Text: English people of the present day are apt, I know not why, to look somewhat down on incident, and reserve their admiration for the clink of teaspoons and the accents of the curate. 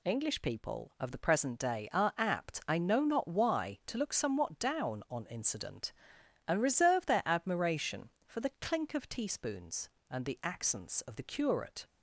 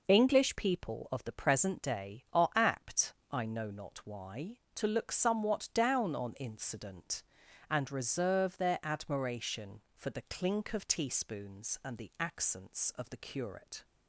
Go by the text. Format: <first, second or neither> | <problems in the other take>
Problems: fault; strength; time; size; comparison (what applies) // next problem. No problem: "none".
neither | none